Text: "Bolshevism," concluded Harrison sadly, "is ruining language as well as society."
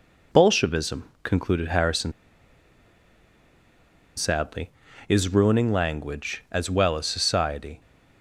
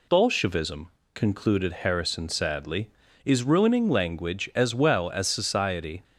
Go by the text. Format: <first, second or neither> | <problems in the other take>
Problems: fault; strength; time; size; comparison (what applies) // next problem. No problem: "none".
second | pauses between "Harrison" and "sadly"; strong; at 2.1 s; 2.0 s long